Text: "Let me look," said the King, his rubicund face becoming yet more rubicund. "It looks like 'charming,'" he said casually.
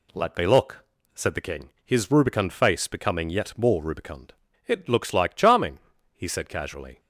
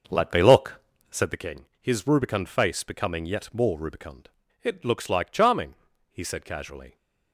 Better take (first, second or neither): first